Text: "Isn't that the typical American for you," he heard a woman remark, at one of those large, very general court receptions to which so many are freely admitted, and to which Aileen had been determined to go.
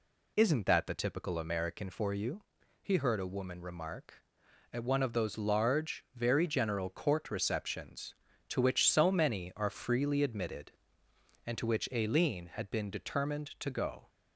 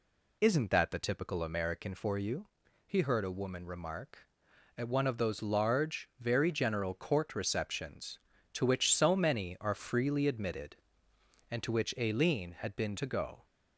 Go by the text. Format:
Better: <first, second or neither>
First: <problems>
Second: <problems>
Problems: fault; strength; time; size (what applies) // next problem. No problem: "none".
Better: first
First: none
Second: skips "determined"; at 12.9 s